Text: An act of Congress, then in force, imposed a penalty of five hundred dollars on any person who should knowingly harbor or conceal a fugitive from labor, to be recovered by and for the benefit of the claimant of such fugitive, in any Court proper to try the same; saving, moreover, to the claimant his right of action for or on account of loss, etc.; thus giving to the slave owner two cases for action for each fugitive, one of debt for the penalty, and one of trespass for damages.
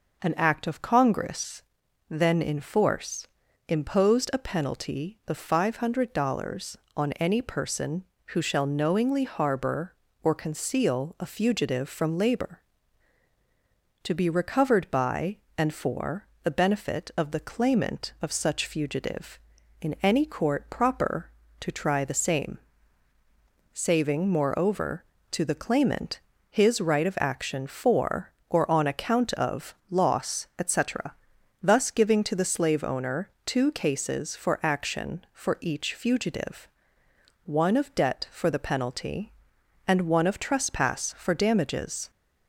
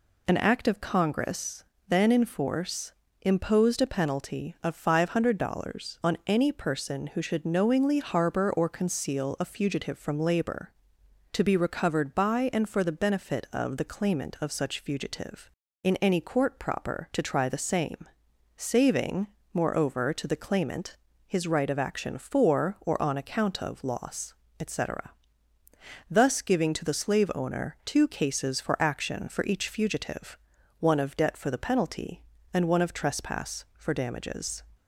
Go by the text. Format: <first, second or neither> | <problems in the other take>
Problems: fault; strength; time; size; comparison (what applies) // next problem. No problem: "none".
second | says "shall" for "should"; at 8.4 s // pauses between "for" and "the"; slight; at 16.2 s; 0.18 s long // pauses between "claimant" and "his"; slight; at 26.1 s; 0.28 s long; slight in the second // pauses between "of" and "loss"; slight; at 29.7 s; 0.16 s long // pauses between "owner" and "two"; slight; at 33.2 s; 0.16 s long